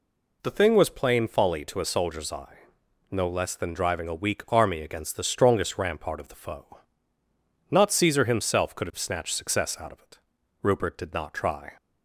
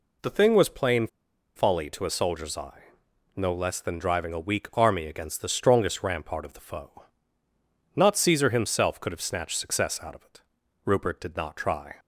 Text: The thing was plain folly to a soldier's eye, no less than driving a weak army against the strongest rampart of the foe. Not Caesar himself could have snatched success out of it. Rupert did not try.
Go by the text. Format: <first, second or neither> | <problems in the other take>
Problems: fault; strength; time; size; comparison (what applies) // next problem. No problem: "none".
first | pauses between "plain" and "folly"; noticeable; at 1.0 s; 0.48 s long